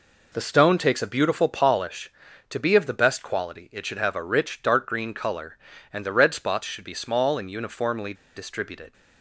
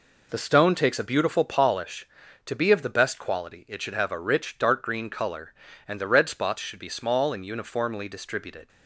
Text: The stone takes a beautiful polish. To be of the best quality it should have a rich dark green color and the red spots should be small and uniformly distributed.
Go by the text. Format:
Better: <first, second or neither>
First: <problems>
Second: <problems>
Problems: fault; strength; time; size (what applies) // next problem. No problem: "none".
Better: second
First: pauses between "uniformly" and "distributed"; slight; at 8.1 s; 0.20 s long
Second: none